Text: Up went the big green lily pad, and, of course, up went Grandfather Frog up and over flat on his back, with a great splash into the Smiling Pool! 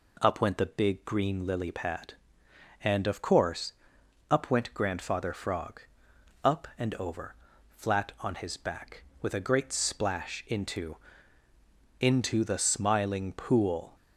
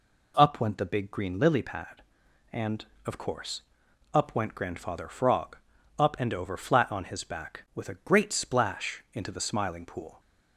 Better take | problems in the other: second | pauses between "Frog" and "up"; noticeable; at 5.8 s; 0.61 s long; also in the second // pauses between "over" and "flat"; slight; at 7.3 s; 0.34 s long // says "into" twice; at 11.9 s

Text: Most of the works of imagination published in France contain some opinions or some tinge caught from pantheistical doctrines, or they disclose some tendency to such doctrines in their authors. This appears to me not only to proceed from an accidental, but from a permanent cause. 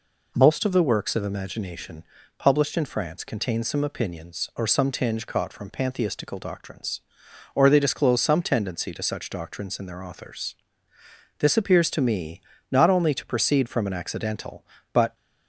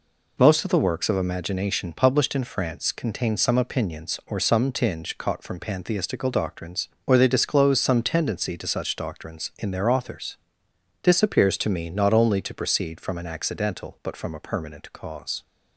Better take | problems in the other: second | pauses between "imagination" and "published"; slight; at 2.0 s; 0.34 s long // pauses between "me" and "not"; slight; at 12.4 s; 0.30 s long // stops before "from a permanent cause"; at 15.1 s

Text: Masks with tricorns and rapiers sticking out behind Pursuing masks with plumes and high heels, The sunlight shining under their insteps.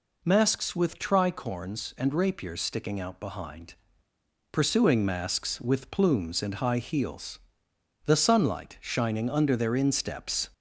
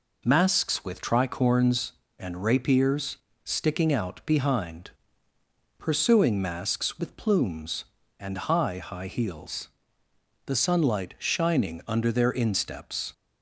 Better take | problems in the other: first | pauses between "rapiers" and "sticking"; slight; at 3.1 s; 0.26 s long // pauses between "behind" and "Pursuing"; noticeable; at 4.9 s; 0.88 s long; noticeable in the first // says "high" twice; at 8.7 s

